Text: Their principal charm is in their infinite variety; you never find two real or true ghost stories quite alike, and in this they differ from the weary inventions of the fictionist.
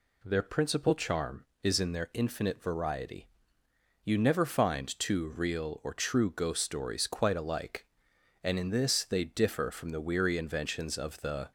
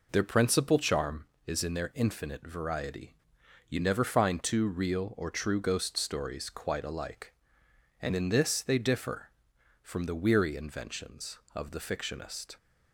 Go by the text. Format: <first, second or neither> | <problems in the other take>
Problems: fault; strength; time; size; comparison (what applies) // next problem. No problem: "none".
second | stops before "fictionist"; at 11.4 s